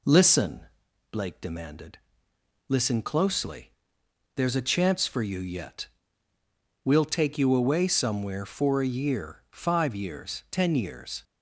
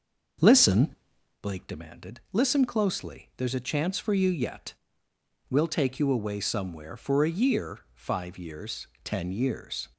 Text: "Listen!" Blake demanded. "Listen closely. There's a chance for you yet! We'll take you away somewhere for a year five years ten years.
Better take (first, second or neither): first